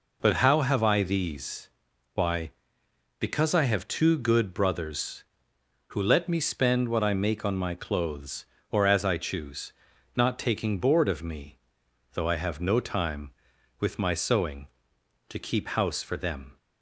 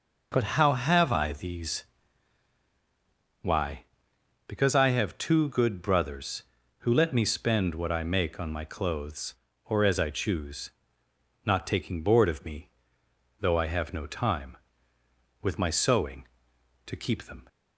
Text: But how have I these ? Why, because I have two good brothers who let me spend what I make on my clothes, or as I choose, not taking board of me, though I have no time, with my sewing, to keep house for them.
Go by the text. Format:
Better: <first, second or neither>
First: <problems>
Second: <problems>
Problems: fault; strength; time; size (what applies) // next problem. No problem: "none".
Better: first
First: none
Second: skips "house for"; at 17.2 s